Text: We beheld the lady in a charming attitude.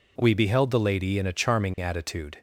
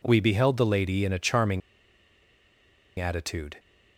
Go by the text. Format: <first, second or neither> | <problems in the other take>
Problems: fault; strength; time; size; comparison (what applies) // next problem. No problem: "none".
first | pauses between "charming" and "attitude"; strong; at 1.6 s; 1.3 s long